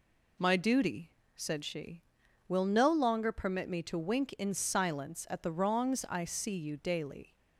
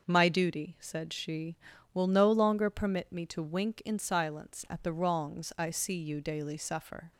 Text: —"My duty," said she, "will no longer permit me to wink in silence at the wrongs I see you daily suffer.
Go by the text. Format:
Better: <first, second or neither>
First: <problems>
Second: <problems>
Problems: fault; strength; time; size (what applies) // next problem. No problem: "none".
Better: second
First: stops before "suffer"; at 7.3 s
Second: none